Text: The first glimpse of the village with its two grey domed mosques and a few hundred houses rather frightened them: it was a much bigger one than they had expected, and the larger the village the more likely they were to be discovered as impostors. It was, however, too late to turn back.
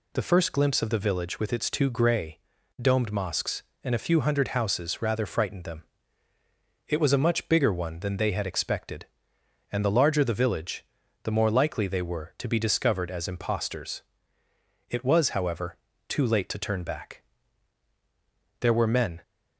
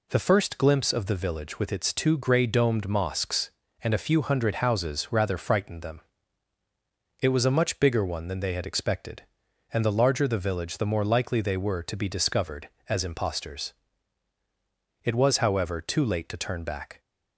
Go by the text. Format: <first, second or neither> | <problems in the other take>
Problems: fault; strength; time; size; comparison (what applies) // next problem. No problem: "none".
second | pauses between "grey" and "domed"; at 2.3 s; 0.42 s long // pauses between "village" and "the"; at 10.8 s; 0.38 s long // goes on to say "There were men"; from 18.6 s on; 0.60 s long